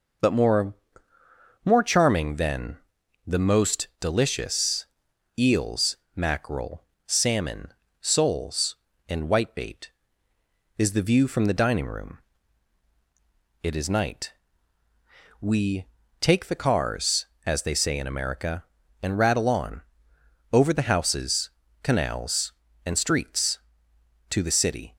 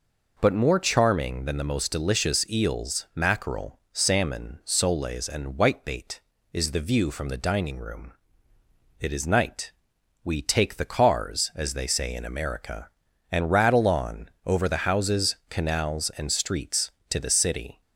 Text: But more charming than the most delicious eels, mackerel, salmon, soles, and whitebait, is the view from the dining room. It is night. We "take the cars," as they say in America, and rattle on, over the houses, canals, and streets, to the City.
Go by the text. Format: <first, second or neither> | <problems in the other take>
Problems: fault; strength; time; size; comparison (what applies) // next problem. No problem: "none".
second | says "more" twice; at 1.6 s // pauses between "than" and "the"; noticeable; at 2.7 s; 0.48 s long // pauses between "delicious" and "eels"; noticeable; at 4.8 s; 0.52 s long // pauses between "We" and "take"; slight; at 15.8 s; 0.36 s long